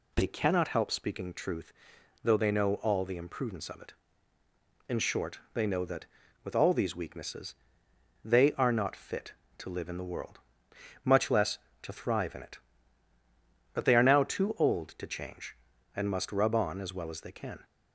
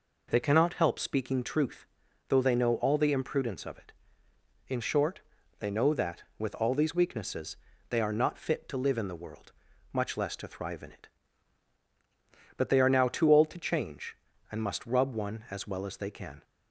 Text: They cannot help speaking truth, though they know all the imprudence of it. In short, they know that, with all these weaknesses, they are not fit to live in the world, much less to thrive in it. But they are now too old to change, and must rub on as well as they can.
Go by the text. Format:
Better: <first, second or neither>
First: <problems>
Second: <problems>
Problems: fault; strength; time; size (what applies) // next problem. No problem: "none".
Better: first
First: none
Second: says "one" for "on"; at 15.1 s